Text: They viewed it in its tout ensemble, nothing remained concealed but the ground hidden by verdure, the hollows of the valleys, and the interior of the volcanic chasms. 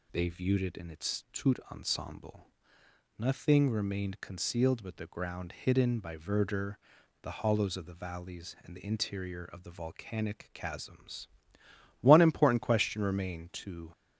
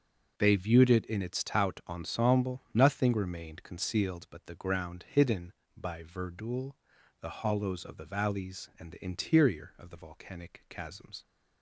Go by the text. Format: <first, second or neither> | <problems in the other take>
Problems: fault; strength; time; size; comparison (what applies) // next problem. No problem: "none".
second | goes on to say "One important question remained to"; strong; from 11.9 s on; 1.9 s long